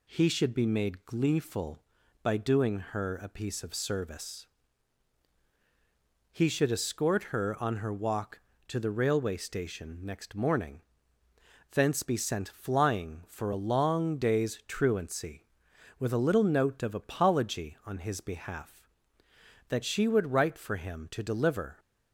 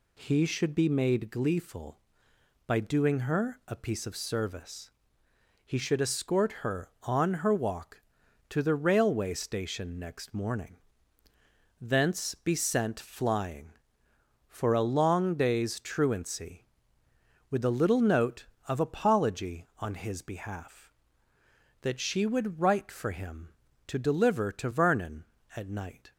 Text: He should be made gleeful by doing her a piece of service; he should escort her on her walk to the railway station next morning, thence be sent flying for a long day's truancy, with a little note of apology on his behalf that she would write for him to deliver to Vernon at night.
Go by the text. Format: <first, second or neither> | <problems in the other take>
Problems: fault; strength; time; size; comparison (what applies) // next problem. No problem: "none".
second | stops before "to Vernon at night"; at 21.7 s